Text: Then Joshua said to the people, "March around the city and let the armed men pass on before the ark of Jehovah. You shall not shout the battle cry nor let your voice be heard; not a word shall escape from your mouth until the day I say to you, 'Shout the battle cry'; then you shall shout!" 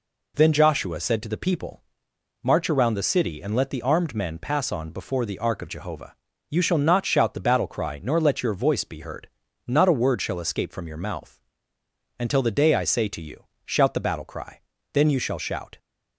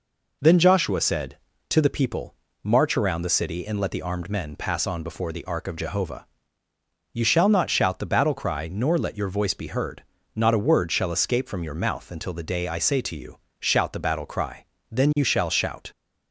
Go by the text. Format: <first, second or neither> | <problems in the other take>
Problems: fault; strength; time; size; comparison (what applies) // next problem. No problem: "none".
second | pauses between "mouth" and "until"; noticeable; at 11.3 s; 0.78 s long